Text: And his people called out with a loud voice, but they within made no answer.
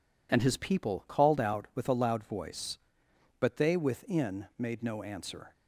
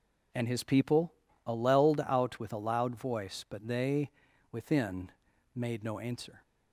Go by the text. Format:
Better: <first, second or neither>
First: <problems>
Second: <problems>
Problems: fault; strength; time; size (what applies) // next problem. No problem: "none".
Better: first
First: none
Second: says "alleled" for "called"; at 1.4 s // pauses between "they" and "within"; at 4.0 s; 0.42 s long // pauses between "within" and "made"; at 5.0 s; 0.44 s long